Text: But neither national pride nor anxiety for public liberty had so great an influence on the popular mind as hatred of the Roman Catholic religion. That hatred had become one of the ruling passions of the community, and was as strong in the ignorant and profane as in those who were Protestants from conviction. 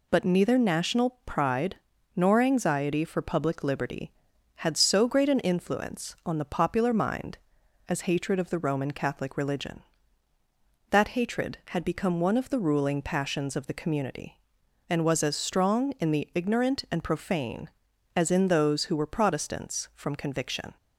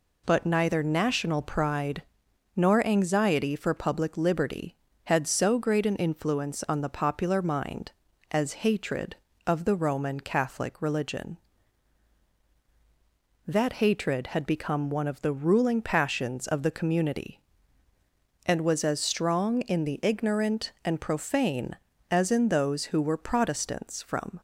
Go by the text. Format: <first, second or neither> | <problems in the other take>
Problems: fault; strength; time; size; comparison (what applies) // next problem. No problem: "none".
first | pauses between "pride" and "nor"; noticeable; at 2.0 s; 0.54 s long; also in the first // stops before "conviction"; at 24.3 s